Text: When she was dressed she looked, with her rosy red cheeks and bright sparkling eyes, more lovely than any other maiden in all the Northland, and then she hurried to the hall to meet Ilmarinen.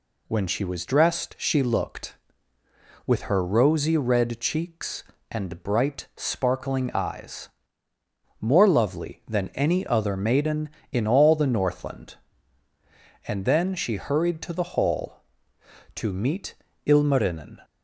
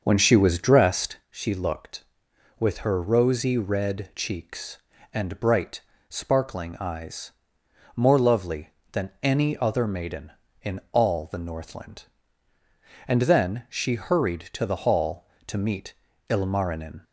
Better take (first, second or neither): first